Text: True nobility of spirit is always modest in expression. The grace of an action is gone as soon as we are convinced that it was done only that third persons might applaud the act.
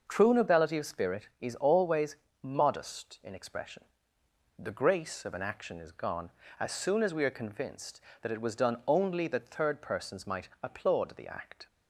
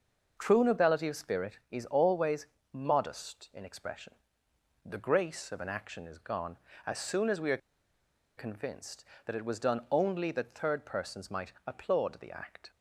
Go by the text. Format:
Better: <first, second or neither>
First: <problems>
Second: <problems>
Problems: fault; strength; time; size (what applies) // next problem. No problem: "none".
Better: first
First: pauses between "always" and "modest"; slight; at 2.1 s; 0.26 s long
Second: pauses between "always" and "modest"; slight; at 2.4 s; 0.26 s long // pauses between "are" and "convinced"; noticeable; at 7.5 s; 0.80 s long